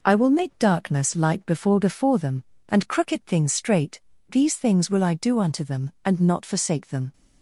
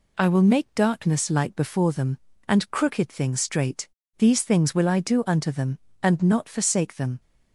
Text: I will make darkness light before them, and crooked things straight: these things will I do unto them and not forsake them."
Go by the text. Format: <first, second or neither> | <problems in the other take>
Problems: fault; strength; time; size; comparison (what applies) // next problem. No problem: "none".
second | says "before" twice; at 1.7 s